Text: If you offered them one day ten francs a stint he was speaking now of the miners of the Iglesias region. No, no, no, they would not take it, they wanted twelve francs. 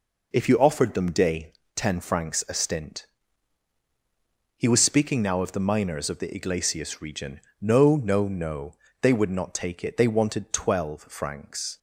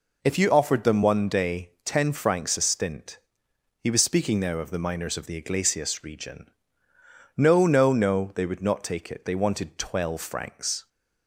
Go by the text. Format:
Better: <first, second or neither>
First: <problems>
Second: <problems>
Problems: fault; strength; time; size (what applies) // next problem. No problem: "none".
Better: second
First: skips "one"; at 1.1 s // pauses between "day" and "ten"; slight; at 1.5 s; 0.24 s long // pauses between "stint" and "he"; strong; at 3.0 s; 1.5 s long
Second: pauses between "stint" and "he"; noticeable; at 3.1 s; 0.62 s long